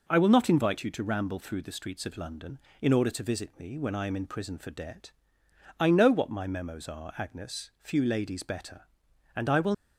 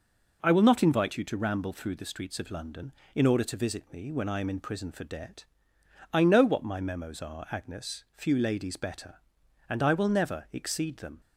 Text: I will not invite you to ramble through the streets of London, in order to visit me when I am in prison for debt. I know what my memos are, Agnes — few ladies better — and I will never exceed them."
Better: second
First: stops before "never exceed them"; at 9.7 s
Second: none

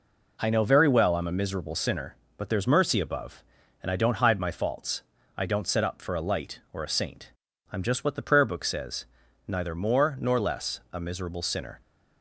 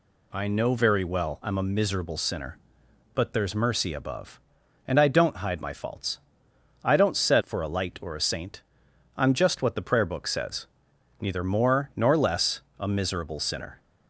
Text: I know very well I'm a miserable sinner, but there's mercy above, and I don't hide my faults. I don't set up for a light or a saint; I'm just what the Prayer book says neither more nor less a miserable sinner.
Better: first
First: pauses between "says" and "neither"; at 9.0 s; 0.42 s long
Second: skips "up"; at 7.4 s // pauses between "says" and "neither"; noticeable; at 10.6 s; 0.54 s long // pauses between "less" and "a"; slight; at 12.6 s; 0.18 s long

